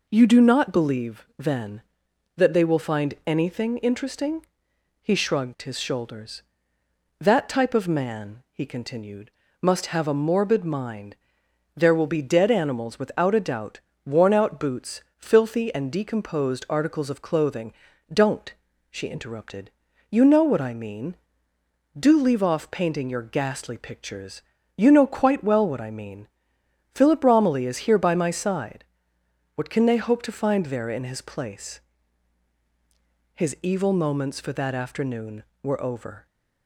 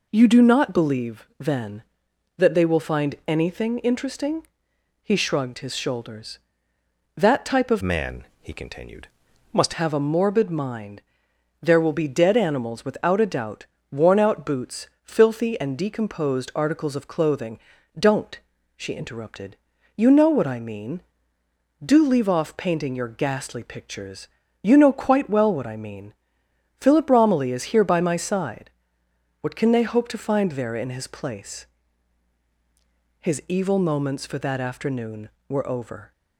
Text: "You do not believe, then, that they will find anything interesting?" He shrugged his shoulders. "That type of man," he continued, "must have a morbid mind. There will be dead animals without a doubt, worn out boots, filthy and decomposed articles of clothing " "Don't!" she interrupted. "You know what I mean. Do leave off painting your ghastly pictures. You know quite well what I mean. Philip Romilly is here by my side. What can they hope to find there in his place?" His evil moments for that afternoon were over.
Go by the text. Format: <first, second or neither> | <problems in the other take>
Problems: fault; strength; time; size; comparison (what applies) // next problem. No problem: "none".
first | changes voice from "man" to "must"; from 7.8 to 9.7 s; 1.9 s long